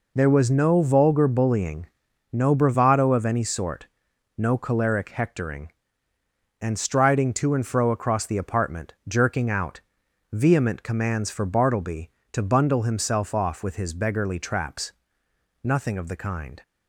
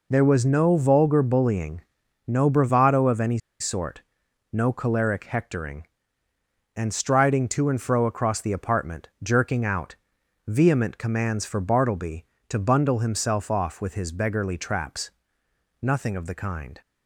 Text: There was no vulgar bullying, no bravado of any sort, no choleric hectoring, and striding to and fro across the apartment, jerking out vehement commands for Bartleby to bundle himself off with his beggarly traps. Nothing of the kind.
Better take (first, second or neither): first